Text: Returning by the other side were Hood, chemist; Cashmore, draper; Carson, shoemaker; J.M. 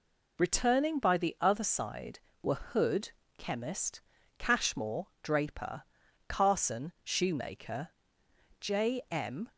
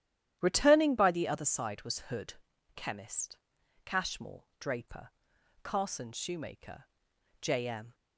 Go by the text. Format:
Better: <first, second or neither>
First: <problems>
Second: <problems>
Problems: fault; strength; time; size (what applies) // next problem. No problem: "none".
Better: first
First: none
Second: starts louder than the rest; strong; until 1.4 s; 11 dB // says "was" for "were"; at 1.8 s